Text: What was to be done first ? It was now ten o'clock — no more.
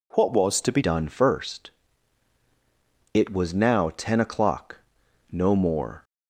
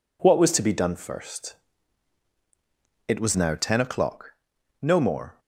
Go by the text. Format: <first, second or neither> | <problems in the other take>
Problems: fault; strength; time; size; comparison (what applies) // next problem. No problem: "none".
second | changes voice at "done"; from 0.8 s on; 5.2 s long